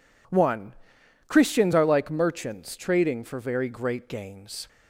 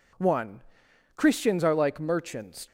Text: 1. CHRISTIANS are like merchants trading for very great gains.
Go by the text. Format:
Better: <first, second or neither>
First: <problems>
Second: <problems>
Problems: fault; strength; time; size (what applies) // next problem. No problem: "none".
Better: first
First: none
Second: stops before "trading for very great gains"; at 2.6 s